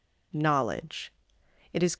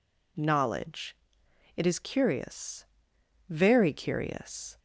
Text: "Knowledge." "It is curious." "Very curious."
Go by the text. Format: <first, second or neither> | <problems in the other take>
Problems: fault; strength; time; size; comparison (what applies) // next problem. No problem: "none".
second | stops before "curious Very curious"; at 1.9 s